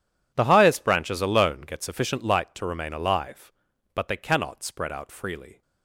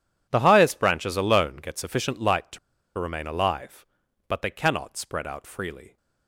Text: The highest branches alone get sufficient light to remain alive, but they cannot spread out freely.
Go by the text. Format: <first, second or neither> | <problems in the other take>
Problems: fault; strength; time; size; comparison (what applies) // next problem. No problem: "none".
first | pauses between "to" and "remain"; at 2.5 s; 0.39 s long